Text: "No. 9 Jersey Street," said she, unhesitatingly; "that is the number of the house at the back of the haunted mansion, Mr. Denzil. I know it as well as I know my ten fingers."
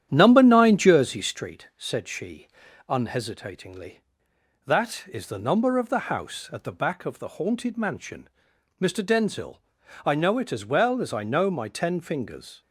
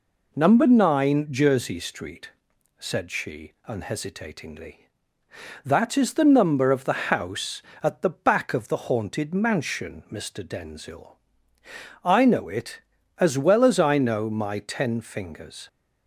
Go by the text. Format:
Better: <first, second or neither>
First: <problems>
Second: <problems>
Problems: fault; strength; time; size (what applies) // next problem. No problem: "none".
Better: second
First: starts louder than the rest; strong; until 1.4 s; 10 dB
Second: none